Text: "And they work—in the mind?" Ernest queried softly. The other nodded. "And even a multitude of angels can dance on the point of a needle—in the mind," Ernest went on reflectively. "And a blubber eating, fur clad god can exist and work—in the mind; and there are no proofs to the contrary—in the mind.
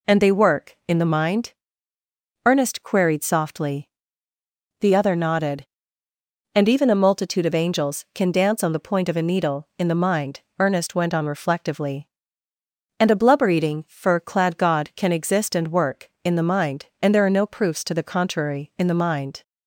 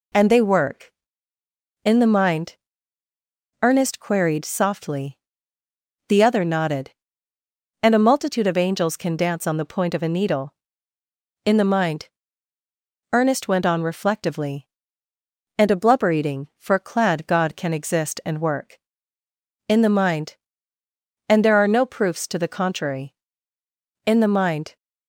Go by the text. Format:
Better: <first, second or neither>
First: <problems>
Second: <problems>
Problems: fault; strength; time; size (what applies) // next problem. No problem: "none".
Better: first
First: none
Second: skips "even"; at 7.9 s